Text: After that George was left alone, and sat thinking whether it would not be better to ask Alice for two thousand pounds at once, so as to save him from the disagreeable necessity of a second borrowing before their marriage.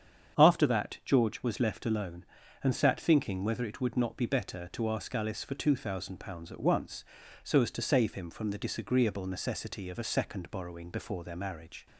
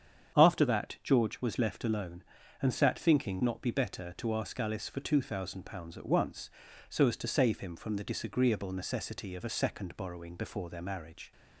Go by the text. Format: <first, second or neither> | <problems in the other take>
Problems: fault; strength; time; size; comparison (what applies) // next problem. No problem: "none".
first | starts louder than the rest; strong; until 1.4 s; 8 dB; strong in the first // skips "whether it would"; at 3.4 s